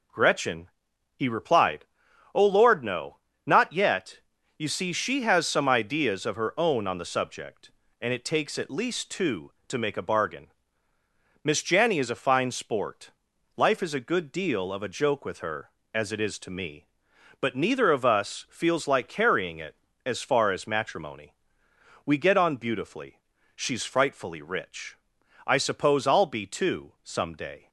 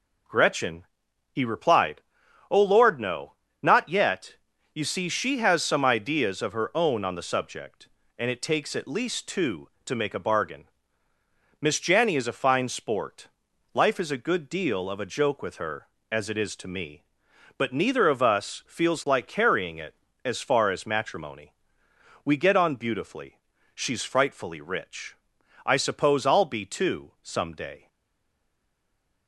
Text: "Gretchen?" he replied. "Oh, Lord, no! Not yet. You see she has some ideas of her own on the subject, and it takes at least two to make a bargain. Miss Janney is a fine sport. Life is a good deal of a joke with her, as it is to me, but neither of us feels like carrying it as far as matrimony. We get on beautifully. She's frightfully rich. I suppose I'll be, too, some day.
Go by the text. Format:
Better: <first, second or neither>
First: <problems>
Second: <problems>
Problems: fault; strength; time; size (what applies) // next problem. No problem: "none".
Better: first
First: none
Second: stays silent after the last word; noticeable; from 27.8 s on; 1.4 s long